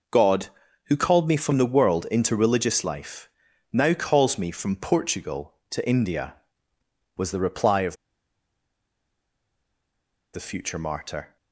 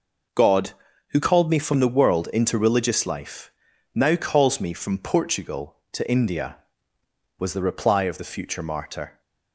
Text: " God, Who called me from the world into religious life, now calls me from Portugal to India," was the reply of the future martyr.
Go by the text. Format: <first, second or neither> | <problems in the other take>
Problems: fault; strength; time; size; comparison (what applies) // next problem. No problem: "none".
second | pauses between "of" and "the"; strong; at 7.9 s; 2.3 s long